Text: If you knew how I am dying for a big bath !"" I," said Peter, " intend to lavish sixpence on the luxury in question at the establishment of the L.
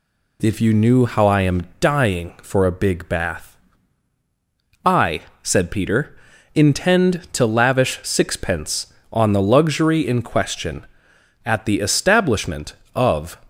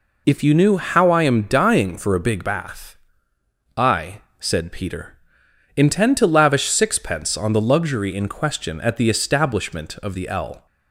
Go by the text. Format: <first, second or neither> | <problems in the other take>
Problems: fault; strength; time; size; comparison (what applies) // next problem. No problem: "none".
second | stops before "the L"; at 13.4 s